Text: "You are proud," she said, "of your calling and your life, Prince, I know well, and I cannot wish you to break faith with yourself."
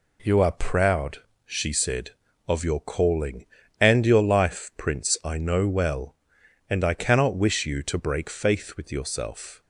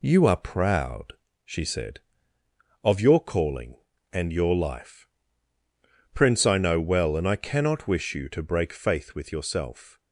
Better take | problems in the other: neither | none

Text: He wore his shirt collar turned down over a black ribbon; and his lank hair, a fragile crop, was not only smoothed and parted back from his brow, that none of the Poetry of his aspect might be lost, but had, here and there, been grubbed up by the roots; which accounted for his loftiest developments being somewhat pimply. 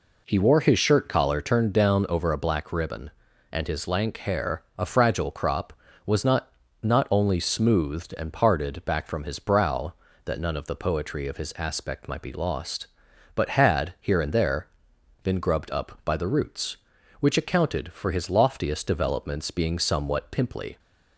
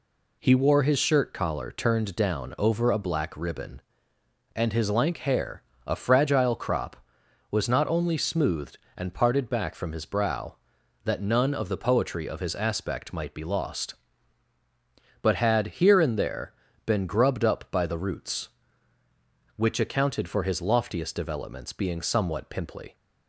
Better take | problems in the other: second | says "not" twice; at 6.8 s

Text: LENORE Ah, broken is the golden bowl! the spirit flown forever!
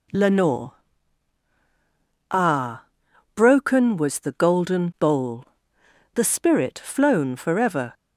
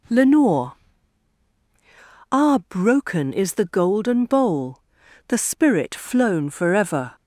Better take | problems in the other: second | pauses between "LENORE" and "Ah"; strong; at 0.7 s; 1.6 s long; strong in the second // says "was" for "is"; at 3.9 s

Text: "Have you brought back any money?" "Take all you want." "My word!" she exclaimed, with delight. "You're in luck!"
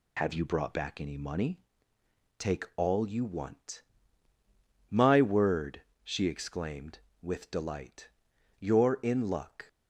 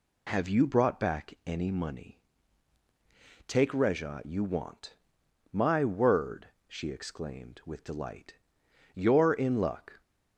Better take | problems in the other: first | says "reja" for "all"; at 3.7 s

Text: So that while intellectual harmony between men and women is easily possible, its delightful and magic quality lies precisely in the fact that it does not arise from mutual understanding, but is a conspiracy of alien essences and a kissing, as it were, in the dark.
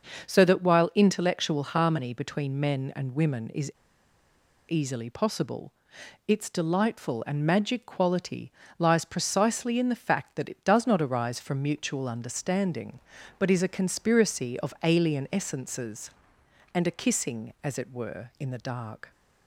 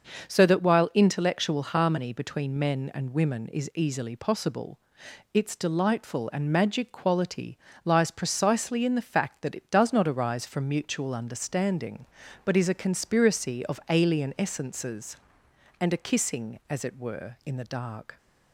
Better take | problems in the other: second | starts louder than the rest; until 1.3 s; 6 dB; noticeable in the second // pauses between "is" and "easily"; noticeable; at 3.7 s; 0.96 s long // pauses between "quality" and "lies"; slight; at 8.5 s; 0.26 s long; slight in the second

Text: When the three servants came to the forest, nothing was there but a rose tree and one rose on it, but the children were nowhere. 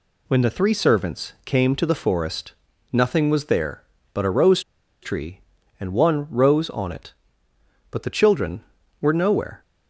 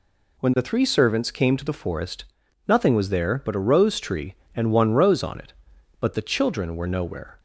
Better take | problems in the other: second | pauses between "rose" and "tree"; at 4.6 s; 0.41 s long

